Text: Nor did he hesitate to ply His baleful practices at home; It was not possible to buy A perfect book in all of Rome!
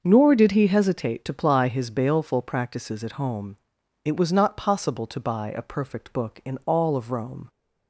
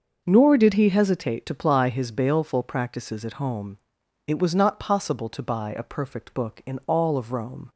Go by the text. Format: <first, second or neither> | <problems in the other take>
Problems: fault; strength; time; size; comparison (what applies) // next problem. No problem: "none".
neither | starts louder than the rest; noticeable; the same in both